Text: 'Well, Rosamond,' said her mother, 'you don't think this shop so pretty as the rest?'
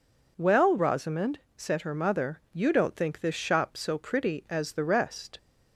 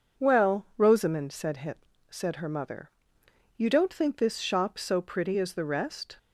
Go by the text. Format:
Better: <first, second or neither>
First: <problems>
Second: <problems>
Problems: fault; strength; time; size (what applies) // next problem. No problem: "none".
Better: first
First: none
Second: says "said" twice; at 2.0 s